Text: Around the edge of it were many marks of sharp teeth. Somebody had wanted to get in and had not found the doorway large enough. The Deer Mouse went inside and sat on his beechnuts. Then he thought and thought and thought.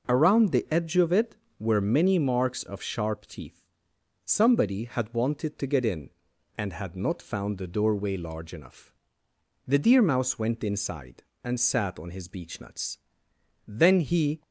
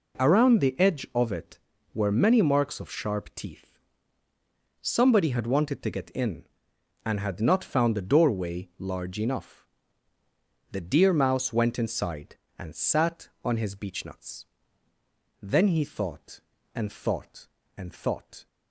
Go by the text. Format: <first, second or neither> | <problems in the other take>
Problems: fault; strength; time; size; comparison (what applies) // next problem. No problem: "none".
second | stops before "thought and thought and thought"; at 14.4 s